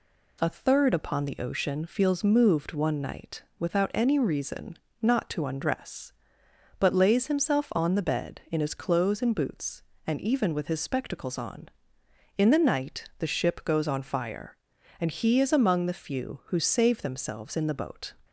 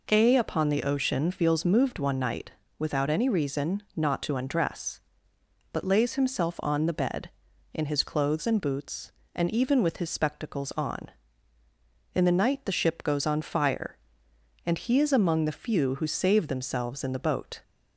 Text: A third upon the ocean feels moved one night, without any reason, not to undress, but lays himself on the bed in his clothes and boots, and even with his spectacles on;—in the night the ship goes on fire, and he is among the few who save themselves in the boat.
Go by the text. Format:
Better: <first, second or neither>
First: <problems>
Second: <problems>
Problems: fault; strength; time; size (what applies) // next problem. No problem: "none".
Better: first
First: none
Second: skips "third"; at 0.3 s